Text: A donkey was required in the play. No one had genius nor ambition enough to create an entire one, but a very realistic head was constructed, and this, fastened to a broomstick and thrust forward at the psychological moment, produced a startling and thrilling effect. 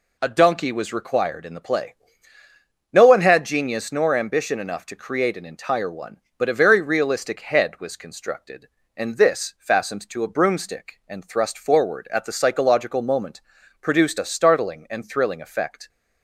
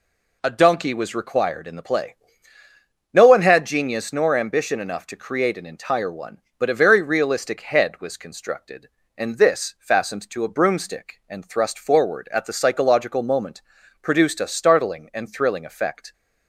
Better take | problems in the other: neither | none

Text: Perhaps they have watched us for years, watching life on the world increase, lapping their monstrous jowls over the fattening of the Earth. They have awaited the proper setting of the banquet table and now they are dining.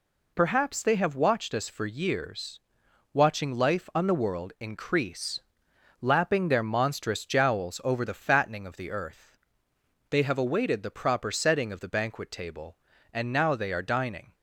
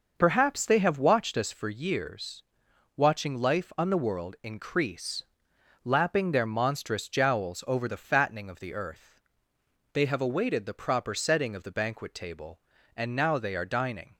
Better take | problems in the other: first | starts louder than the rest; noticeable; until 1.6 s; 6 dB

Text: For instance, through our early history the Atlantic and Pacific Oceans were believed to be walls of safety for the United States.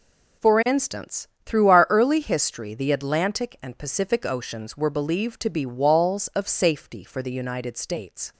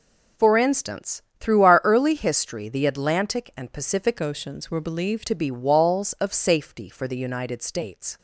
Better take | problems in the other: first | changes voice from "Oceans" to "believed"; from 4.2 to 5.2 s; 1.0 s long

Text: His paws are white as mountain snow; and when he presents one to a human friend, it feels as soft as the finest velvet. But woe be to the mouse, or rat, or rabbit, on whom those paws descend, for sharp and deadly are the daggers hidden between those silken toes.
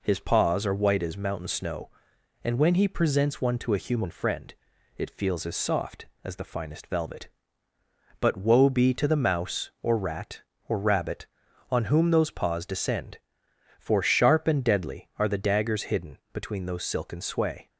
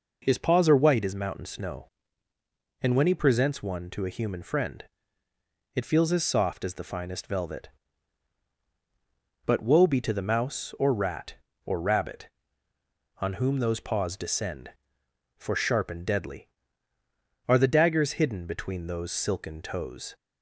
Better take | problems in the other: second | pauses between "hidden" and "between"; slight; at 16.1 s; 0.16 s long // says "sway" for "toes"; at 17.2 s

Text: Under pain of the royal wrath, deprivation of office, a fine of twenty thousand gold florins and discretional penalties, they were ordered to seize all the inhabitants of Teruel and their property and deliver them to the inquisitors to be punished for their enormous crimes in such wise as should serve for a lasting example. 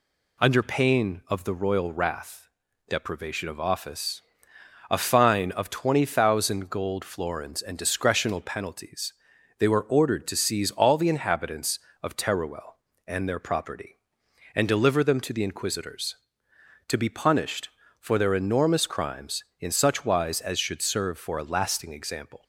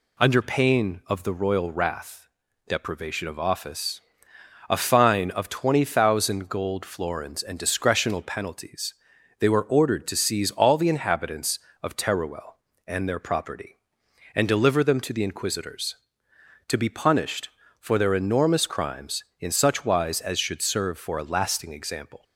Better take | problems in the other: neither | none

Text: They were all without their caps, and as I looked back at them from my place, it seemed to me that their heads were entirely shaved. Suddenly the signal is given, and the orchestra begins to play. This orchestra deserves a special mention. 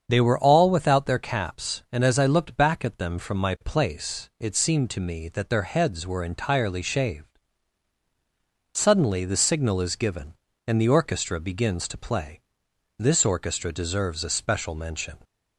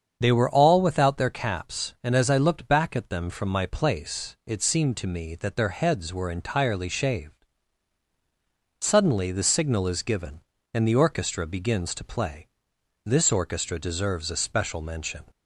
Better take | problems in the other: neither | starts louder than the rest; strong; the same in both

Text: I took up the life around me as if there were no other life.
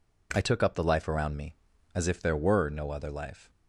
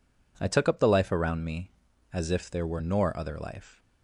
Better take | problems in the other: first | says "nor" for "no"; at 2.8 s

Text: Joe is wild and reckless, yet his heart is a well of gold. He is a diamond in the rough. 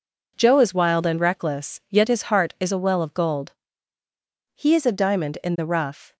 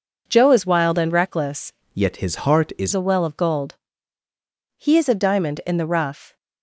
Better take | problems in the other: first | changes voice from "yet" to "is"; from 1.9 to 2.9 s; 1.0 s long

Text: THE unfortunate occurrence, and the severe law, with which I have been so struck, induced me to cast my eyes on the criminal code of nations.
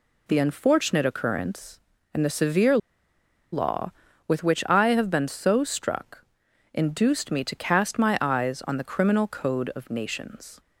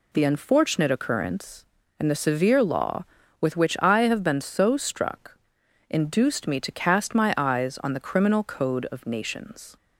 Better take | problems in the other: second | pauses between "severe" and "law"; noticeable; at 2.7 s; 0.75 s long

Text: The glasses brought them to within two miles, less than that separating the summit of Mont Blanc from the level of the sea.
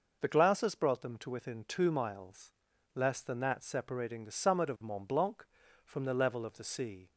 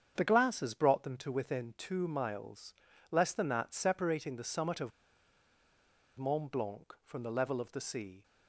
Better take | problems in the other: first | starts louder than the rest; strong; until 1.1 s; 7.5 dB // pauses between "of" and "Mont"; strong; at 4.9 s; 1.2 s long

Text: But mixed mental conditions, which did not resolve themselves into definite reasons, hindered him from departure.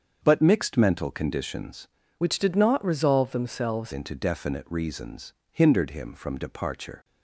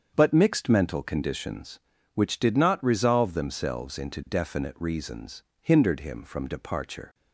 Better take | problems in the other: second | starts louder than the rest; until 1.2 s; 7 dB; strong in the second // changes voice from "which" to "themselves"; from 2.1 to 3.9 s; 1.8 s long

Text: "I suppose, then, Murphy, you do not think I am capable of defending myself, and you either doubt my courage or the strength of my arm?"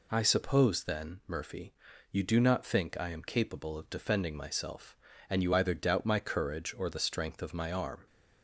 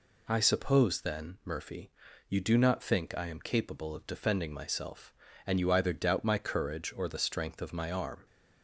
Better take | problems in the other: neither | none

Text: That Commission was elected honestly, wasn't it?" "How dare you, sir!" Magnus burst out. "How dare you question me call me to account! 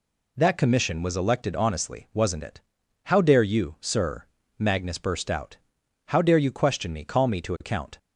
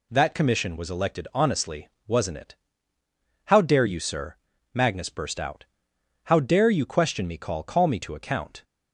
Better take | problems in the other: first | says "call" twice; at 7.6 s

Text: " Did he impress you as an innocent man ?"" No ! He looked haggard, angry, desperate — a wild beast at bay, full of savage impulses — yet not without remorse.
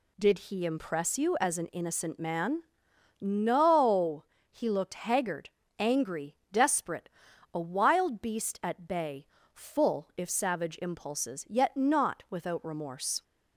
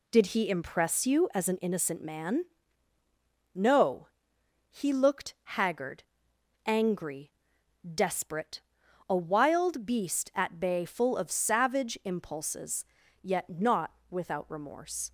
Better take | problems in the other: second | says "if" for "of"; at 10.1 s

